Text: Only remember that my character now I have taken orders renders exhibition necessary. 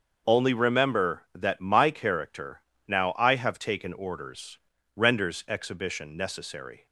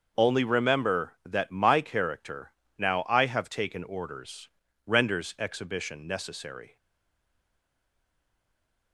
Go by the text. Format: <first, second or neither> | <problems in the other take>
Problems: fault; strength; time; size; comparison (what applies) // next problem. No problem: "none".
first | starts louder than the rest; noticeable; until 1.2 s; 6 dB; noticeable in the first // pauses between "character" and "now"; slight; at 2.5 s; 0.26 s long; slight in the first // pauses between "orders" and "renders"; at 4.4 s; 0.38 s long; also in the first // stays silent after the last word; from 6.7 s on; 2.2 s long